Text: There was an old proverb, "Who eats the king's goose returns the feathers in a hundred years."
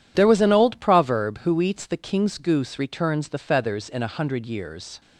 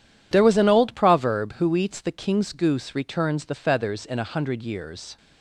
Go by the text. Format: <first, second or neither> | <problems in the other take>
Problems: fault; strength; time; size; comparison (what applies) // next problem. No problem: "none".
neither | none